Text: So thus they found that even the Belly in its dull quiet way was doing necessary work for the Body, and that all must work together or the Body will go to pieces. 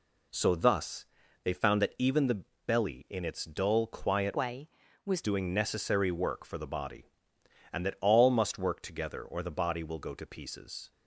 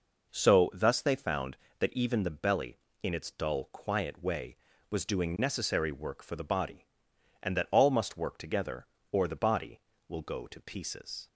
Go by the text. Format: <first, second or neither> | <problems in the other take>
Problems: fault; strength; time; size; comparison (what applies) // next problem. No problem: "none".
second | pauses between "thus" and "they"; at 1.0 s; 0.38 s long // pauses between "the" and "Belly"; slight; at 2.4 s; 0.24 s long // changes voice from "way" to "was"; from 4.3 to 5.2 s; 0.9 s long